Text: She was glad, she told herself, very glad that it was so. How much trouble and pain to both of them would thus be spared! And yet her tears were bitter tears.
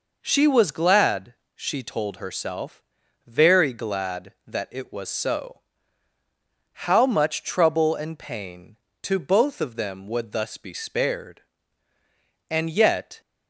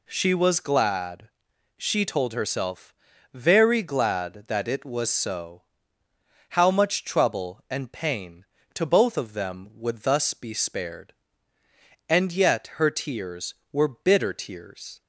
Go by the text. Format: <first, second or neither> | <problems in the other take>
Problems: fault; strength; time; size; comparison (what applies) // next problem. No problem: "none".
second | stops before "her tears were bitter tears"; at 13.2 s